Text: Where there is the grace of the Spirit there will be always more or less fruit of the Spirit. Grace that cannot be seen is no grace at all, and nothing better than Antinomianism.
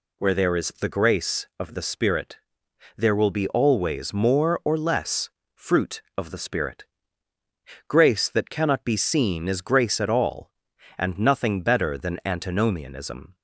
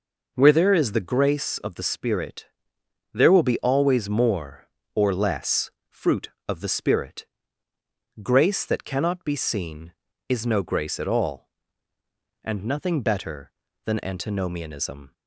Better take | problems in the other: second | pauses between "Spirit" and "there"; noticeable; at 2.3 s; 0.58 s long; noticeable in the second // pauses between "less" and "fruit"; slight; at 5.2 s; 0.26 s long; slight in the second // skips "no"; at 9.6 s

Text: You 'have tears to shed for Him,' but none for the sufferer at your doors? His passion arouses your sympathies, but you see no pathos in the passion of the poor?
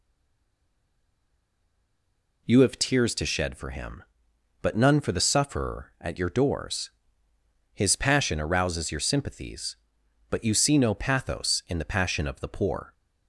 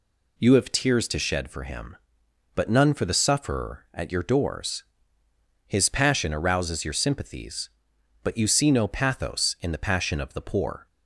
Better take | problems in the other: second | stays silent before the first word; until 2.4 s; 2.4 s long

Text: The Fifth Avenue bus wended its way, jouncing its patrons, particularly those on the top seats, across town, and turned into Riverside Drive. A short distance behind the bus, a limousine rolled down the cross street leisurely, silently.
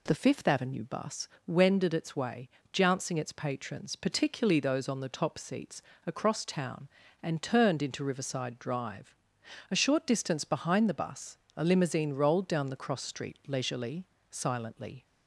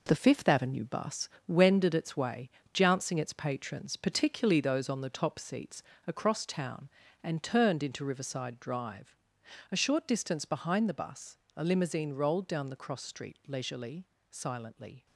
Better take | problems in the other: first | gets quieter; strong; throughout; 8 dB // pauses between "bus" and "wended"; slight; at 1.2 s; 0.22 s long; slight in the first

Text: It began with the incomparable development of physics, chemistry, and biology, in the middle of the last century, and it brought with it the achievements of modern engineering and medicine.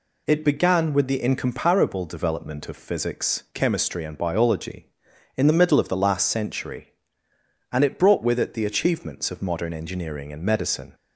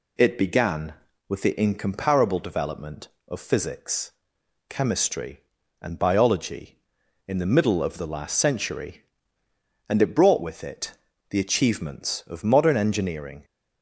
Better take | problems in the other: first | pauses between "it" and "the"; slight; at 10.9 s; 0.36 s long // stops before "and medicine"; at 13.4 s

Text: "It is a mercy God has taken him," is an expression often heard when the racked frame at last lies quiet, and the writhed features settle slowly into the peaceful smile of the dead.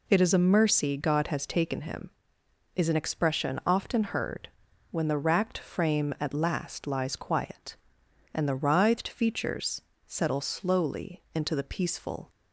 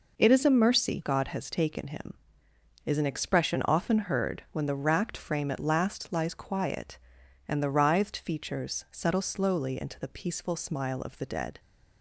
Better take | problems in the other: second | pauses between "heard" and "when"; at 4.4 s; 0.42 s long // pauses between "features" and "settle"; slight; at 9.8 s; 0.24 s long // stops before "smile of the dead"; at 12.2 s

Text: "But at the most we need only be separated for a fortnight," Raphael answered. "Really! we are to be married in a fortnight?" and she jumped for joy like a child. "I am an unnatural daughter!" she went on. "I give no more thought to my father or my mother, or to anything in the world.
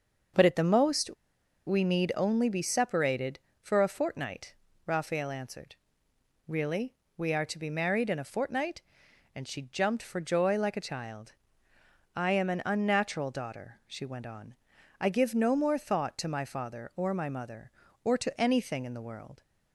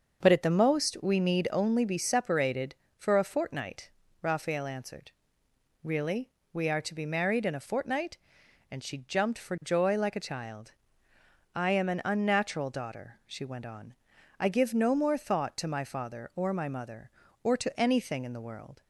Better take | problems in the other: second | starts louder than the rest; until 1.9 s; 6.5 dB; also in the second // pauses between "most" and "we"; noticeable; at 1.0 s; 0.57 s long

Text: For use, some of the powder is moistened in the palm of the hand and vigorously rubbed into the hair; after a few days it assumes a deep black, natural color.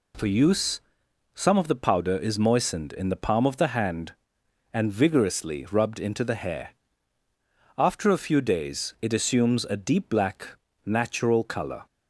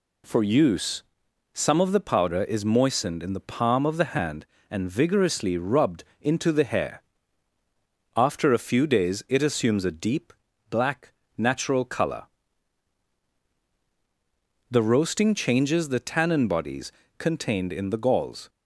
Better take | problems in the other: first | pauses between "rubbed" and "into"; slight; at 6.0 s; 0.16 s long // pauses between "deep" and "black"; at 10.3 s; 0.38 s long // goes on to say "The roasting changes the tannin bodies contained in the galls"; strong; from 14.7 s on; 3.7 s long

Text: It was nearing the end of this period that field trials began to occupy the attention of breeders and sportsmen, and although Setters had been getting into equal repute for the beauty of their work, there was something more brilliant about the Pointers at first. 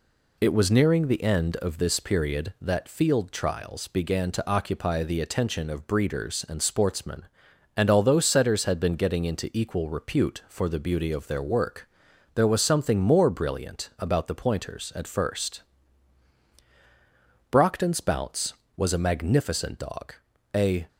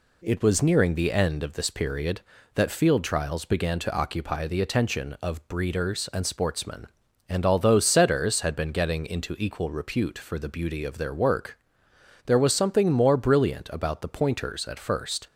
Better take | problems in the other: second | goes on to say "Brockton's Bounce was a magnificent dog a"; strong; from 17.4 s on; 3.3 s long

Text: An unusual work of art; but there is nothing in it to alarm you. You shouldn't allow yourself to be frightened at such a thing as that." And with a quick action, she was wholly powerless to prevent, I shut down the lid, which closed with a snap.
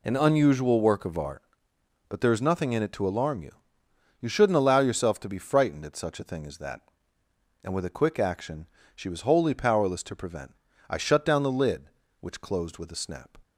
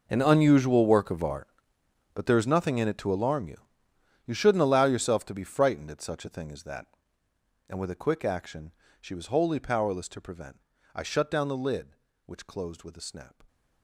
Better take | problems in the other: first | gets quieter; strong; throughout; 18 dB

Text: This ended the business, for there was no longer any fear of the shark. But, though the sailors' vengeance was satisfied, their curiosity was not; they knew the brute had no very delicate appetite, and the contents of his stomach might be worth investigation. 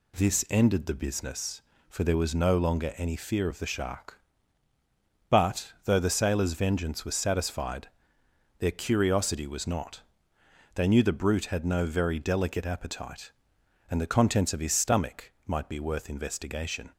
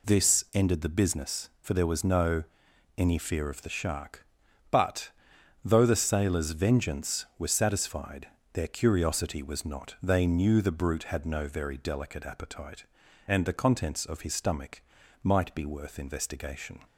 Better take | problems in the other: first | skips "longer"; at 2.6 s // pauses between "stomach" and "might"; at 14.8 s; 0.40 s long; slight in the first

